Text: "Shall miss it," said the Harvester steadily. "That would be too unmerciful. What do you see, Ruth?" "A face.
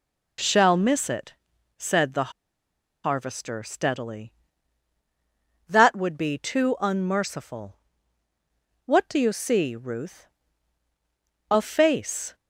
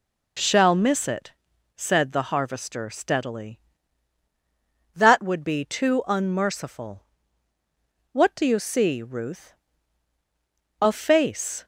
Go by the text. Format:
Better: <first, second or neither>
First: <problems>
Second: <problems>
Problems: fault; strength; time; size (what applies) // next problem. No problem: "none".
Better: second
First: pauses between "the" and "Harvester"; noticeable; at 2.3 s; 0.72 s long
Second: none